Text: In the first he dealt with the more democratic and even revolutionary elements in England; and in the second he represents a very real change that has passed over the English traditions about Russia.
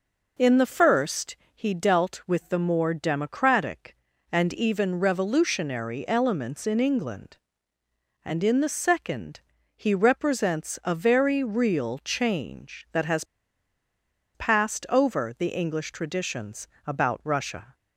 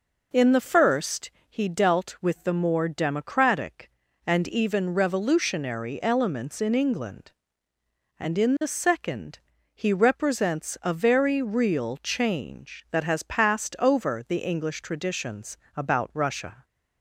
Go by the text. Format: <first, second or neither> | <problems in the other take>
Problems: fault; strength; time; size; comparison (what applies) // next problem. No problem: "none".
second | pauses between "first" and "he"; slight; at 1.3 s; 0.20 s long; slight in the second // pauses between "second" and "he"; slight; at 9.3 s; 0.36 s long; slight in the second // pauses between "has" and "passed"; at 13.2 s; 1.1 s long // pauses between "traditions" and "about"; slight; at 16.6 s; 0.18 s long; slight in the second